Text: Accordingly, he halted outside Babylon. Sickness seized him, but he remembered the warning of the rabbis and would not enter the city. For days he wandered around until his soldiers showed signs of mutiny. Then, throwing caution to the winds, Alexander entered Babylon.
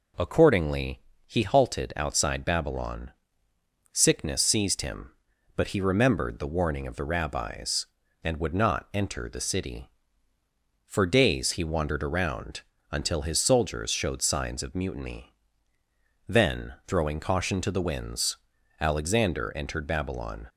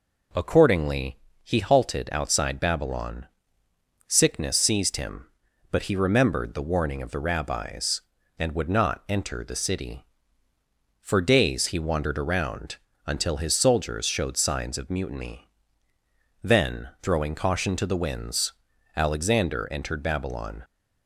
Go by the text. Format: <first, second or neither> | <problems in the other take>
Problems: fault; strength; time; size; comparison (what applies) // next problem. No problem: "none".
neither | pauses between "around" and "until"; slight; the same in both